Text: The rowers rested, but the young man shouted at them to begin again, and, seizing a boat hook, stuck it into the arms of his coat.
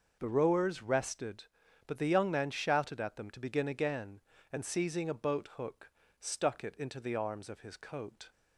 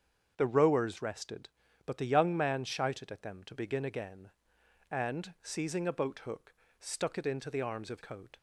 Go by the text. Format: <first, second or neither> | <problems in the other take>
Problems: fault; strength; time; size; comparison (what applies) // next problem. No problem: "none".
first | starts louder than the rest; strong; until 1.3 s; 7 dB // skips "his"; at 8.0 s